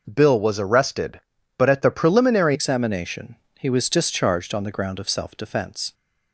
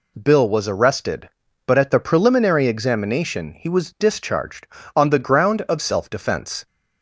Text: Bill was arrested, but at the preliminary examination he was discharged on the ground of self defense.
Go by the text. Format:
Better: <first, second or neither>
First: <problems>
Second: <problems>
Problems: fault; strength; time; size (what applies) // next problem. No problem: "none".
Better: second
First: changes voice at "examination"; from 2.5 s on; 3.4 s long // pauses between "examination" and "he"; slight; at 3.3 s; 0.24 s long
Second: none